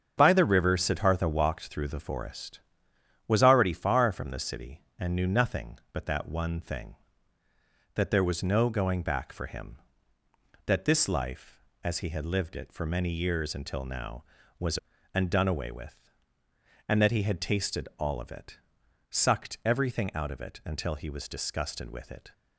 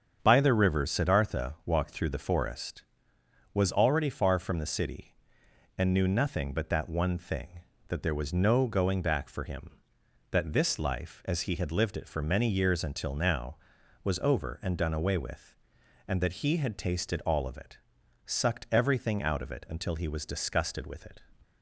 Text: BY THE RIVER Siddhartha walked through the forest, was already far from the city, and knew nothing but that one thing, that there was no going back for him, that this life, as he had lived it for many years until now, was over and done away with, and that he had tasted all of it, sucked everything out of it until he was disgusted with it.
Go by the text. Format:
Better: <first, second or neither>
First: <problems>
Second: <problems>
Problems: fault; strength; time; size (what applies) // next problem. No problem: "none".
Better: second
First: starts louder than the rest; strong; until 1.1 s; 7.5 dB // skips "over"; at 14.9 s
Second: starts louder than the rest; strong; until 1.2 s; 7.5 dB